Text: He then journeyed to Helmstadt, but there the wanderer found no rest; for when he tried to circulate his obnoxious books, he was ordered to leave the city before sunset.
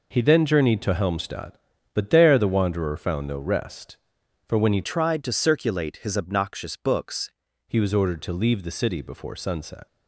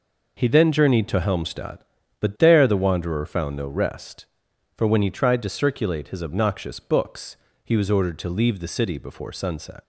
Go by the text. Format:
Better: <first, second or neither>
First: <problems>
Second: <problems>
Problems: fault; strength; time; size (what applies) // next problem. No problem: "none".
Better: second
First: changes voice from "tried" to "books"; from 4.8 to 7.3 s; 2.5 s long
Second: none